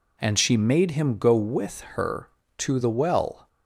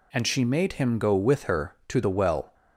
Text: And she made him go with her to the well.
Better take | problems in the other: neither | none

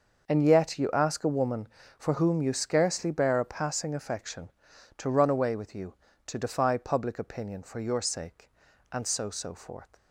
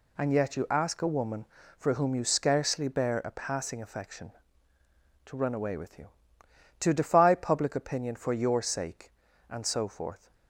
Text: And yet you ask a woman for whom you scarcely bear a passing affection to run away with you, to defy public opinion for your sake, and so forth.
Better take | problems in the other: second | starts louder than the rest; noticeable; until 1.3 s; 6 dB // says "so" twice; at 9.2 s

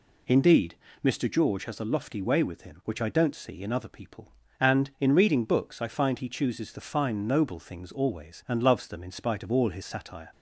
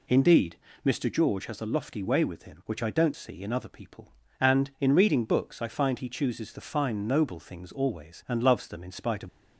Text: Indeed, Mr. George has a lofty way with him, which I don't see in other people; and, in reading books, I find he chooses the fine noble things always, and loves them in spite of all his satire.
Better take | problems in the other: first | stops before "all his satire"; at 9.2 s

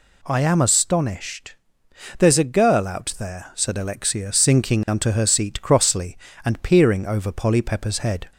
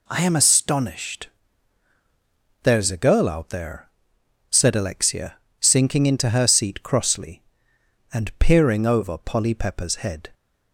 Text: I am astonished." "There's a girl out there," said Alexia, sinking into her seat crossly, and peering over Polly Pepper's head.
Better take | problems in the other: second | says "unto" for "into"; at 4.8 s

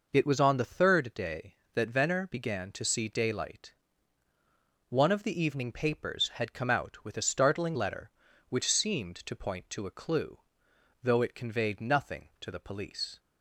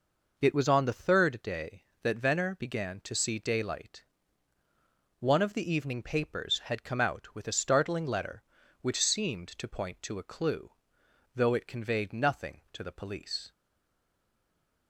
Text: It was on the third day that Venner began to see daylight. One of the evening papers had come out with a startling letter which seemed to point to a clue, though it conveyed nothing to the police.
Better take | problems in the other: first | stays silent after the last word; noticeable; from 13.5 s on; 1.3 s long

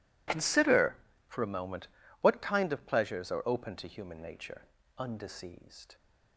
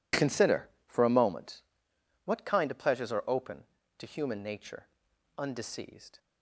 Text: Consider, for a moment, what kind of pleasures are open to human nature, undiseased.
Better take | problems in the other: neither | none

